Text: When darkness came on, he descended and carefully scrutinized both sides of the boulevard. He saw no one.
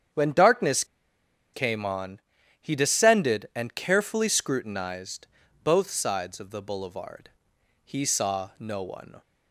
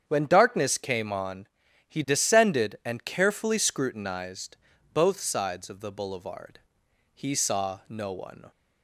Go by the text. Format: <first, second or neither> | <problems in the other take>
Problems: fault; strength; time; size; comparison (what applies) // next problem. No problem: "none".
second | starts louder than the rest; strong; until 1.8 s; 8 dB; strong in the second // pauses between "darkness" and "came"; noticeable; at 0.8 s; 0.69 s long // pauses between "scrutinized" and "both"; at 5.2 s; 0.38 s long; also in the second